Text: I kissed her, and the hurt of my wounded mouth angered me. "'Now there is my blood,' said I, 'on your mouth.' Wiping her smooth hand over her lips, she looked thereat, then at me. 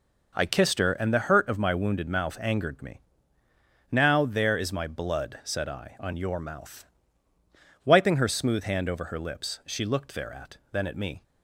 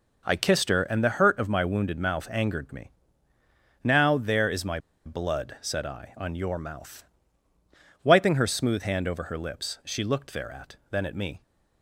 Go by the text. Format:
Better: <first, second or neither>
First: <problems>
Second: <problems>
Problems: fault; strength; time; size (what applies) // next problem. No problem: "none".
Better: first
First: none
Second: pauses between "my" and "blood"; slight; at 4.7 s; 0.26 s long